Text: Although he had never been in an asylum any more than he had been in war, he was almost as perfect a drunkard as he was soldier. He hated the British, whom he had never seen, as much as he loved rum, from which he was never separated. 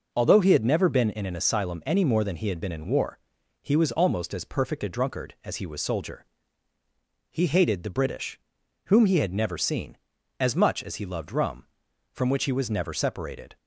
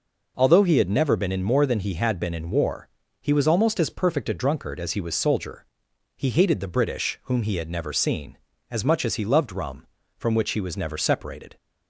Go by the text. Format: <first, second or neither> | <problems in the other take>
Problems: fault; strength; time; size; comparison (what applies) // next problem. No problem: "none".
first | skips "an asylum any"; at 1.4 s